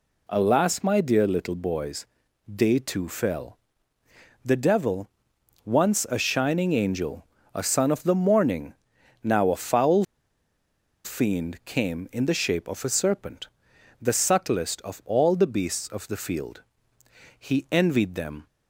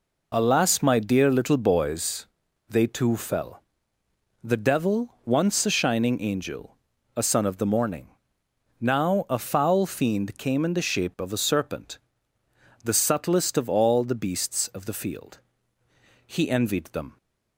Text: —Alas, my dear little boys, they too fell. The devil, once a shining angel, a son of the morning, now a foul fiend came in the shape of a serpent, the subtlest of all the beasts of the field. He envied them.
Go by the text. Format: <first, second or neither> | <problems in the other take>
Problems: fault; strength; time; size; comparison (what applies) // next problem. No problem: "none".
second | pauses between "foul" and "fiend"; at 10.0 s; 1.0 s long